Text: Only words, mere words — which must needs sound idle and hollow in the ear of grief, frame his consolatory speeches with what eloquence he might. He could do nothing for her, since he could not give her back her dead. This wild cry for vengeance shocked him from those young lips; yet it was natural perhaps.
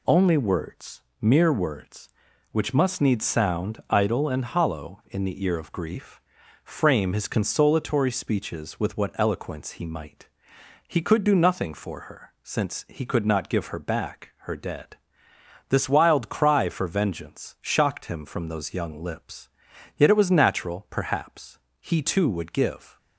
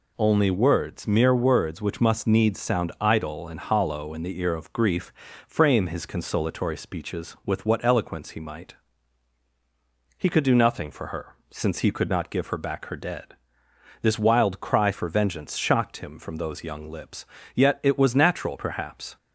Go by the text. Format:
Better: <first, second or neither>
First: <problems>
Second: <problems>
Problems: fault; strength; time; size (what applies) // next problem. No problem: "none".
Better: second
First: goes on to say "He too would give"; noticeable; from 21.8 s on; 1.1 s long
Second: none